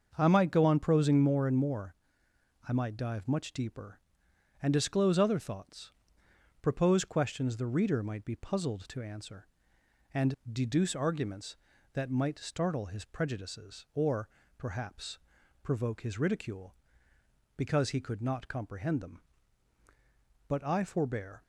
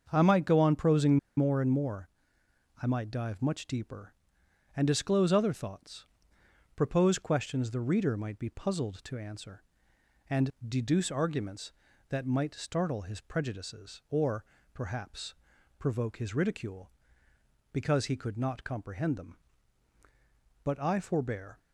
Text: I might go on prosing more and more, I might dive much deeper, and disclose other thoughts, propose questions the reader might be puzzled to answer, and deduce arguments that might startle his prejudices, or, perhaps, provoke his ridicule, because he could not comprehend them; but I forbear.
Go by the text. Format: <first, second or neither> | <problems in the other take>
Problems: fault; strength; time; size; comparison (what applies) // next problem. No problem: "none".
first | starts louder than the rest; until 1.1 s; 6.5 dB; also in the first // pauses between "prosing" and "more"; slight; at 1.1 s; 0.20 s long // pauses between "and" and "deduce"; slight; at 10.4 s; 0.18 s long; slight in the first